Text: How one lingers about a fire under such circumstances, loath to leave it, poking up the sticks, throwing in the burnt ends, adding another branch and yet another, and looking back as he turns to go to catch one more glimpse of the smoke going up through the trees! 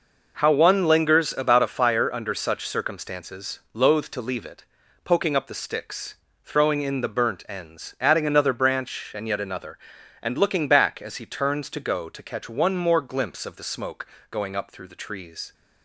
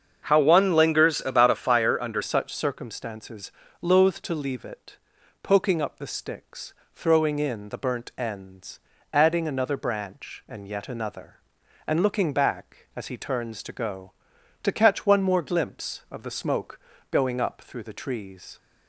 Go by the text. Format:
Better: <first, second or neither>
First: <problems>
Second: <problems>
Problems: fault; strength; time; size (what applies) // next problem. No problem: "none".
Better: first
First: pauses between "smoke" and "going"; slight; at 14.0 s; 0.24 s long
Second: starts louder than the rest; strong; until 1.3 s; 7 dB // changes voice at "such"; from 2.2 s on; 16.3 s long // pauses between "smoke" and "going"; slight; at 16.7 s; 0.32 s long